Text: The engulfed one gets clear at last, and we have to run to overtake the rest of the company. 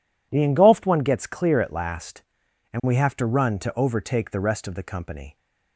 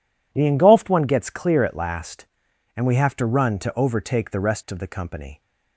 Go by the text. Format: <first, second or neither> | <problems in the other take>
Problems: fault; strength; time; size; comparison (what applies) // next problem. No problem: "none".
neither | none